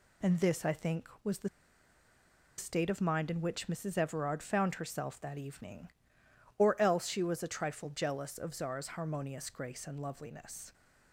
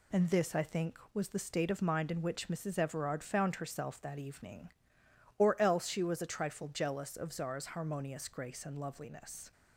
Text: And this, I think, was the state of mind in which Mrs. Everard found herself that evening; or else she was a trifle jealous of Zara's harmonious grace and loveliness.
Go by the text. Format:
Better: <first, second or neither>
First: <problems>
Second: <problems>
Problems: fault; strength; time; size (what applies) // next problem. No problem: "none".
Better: second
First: pauses between "the" and "state"; at 1.4 s; 1.1 s long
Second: none